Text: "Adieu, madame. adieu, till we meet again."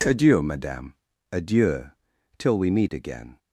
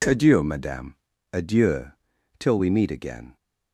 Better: neither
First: none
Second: none

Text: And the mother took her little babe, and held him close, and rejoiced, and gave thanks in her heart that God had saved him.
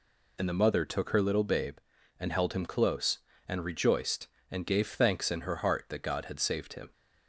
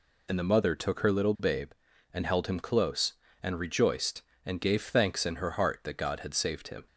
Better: neither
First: none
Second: none

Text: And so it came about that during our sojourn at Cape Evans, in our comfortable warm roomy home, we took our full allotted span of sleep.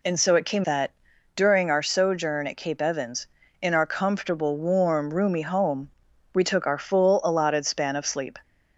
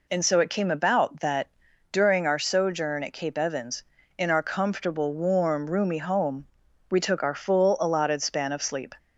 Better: second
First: skips "about"; at 0.6 s // pauses between "that" and "during"; at 0.9 s; 0.42 s long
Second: pauses between "that" and "during"; at 1.4 s; 0.42 s long

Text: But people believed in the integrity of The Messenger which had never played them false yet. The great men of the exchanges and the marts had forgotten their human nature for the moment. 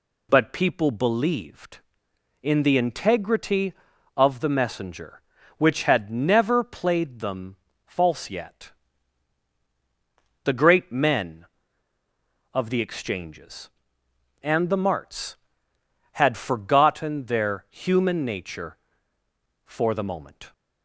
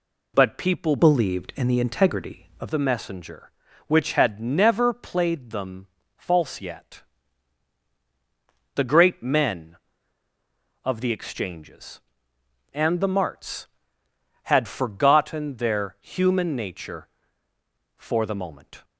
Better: first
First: pauses between "them" and "false"; slight; at 7.5 s; 0.28 s long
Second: changes voice from "believed" to "of"; from 0.9 to 2.7 s; 1.8 s long // pauses between "them" and "false"; slight; at 5.8 s; 0.28 s long

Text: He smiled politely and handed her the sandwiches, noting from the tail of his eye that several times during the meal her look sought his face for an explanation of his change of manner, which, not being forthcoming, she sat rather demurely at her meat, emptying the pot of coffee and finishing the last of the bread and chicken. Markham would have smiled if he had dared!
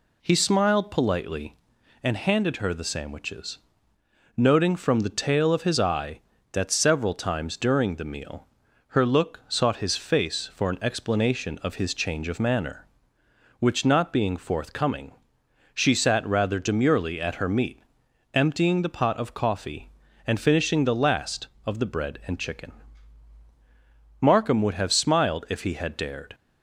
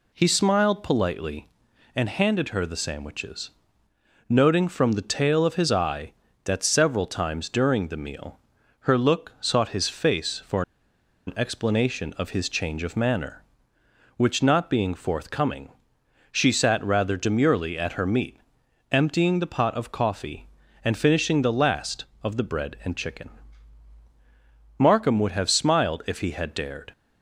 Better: first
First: pauses between "meal" and "her"; at 8.4 s; 0.42 s long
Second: pauses between "meal" and "her"; at 8.3 s; 0.42 s long // pauses between "for" and "an"; noticeable; at 10.6 s; 0.65 s long

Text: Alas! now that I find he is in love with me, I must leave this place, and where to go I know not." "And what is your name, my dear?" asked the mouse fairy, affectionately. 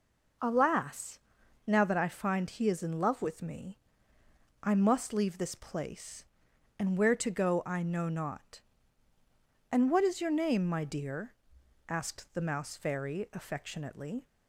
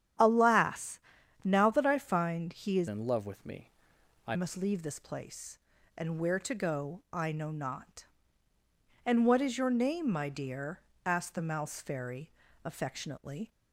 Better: first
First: none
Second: starts louder than the rest; strong; until 1.6 s; 10 dB // changes voice from "in" to "I"; from 2.8 to 4.3 s; 1.5 s long

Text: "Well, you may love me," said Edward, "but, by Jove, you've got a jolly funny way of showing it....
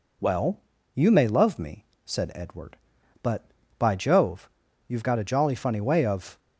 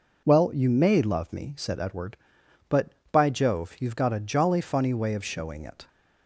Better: second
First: stops before "showing it"; at 6.3 s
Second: none

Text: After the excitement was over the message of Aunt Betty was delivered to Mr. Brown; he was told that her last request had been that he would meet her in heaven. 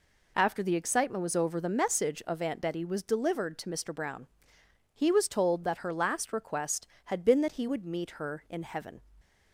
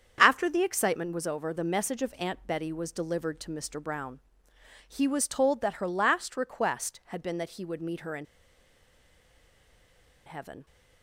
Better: first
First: none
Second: starts louder than the rest; strong; until 1.2 s; 7.5 dB // pauses between "in" and "heaven"; strong; at 8.2 s; 2.0 s long

